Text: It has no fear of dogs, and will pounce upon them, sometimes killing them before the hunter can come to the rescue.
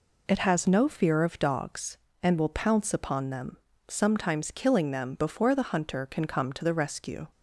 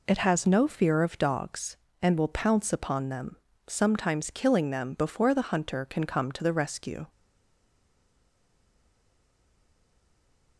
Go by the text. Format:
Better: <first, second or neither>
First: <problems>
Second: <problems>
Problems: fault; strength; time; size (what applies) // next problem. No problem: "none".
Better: first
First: none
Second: stays silent after the last word; strong; from 7.0 s on; 3.5 s long